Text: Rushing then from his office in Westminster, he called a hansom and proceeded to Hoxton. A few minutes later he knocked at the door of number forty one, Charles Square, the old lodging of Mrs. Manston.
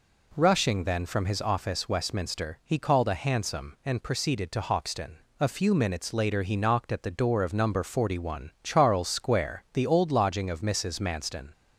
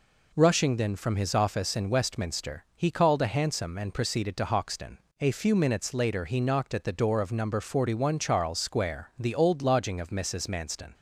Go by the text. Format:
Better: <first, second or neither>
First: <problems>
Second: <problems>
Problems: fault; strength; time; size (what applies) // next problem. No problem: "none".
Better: second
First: skips "in"; at 1.8 s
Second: none